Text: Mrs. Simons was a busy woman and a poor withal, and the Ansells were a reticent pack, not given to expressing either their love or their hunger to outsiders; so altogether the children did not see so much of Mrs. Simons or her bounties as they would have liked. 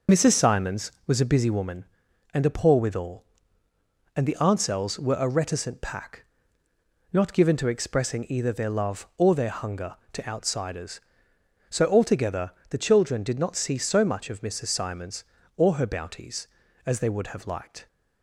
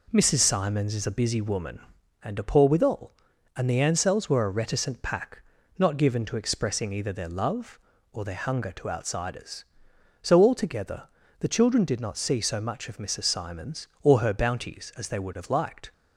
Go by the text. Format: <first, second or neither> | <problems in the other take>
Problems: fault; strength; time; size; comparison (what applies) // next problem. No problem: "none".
first | says "is" for "was"; at 0.9 s // pauses between "altogether" and "the"; at 11.0 s; 0.38 s long; slight in the first